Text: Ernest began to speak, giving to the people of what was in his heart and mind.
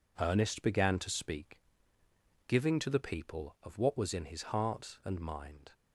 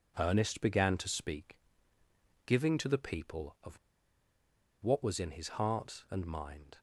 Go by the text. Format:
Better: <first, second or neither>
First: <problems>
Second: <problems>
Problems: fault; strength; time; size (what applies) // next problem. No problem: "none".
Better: first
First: none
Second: pauses between "of" and "what"; at 3.7 s; 1.0 s long